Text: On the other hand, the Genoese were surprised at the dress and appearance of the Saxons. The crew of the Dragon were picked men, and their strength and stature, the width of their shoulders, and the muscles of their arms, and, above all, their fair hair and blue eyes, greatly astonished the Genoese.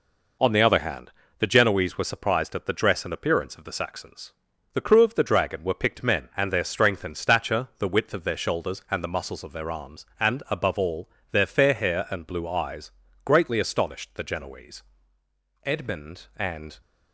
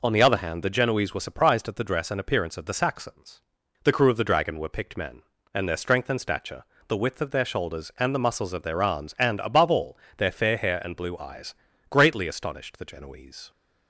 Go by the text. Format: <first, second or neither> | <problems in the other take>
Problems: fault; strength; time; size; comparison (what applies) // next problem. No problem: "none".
second | goes on to say "Edmund and"; noticeable; from 15.6 s on; 1.1 s long